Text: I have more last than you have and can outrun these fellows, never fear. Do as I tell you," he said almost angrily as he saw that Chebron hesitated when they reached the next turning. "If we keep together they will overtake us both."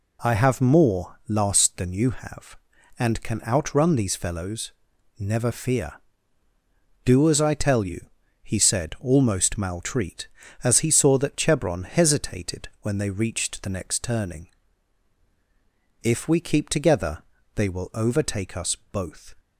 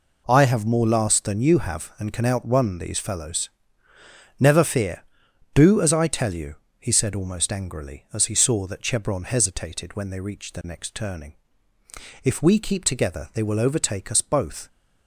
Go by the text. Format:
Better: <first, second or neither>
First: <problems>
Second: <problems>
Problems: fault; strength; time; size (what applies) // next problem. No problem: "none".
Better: second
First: says "maltreat" for "angrily"; at 9.5 s // pauses between "together" and "they"; slight; at 17.2 s; 0.33 s long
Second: none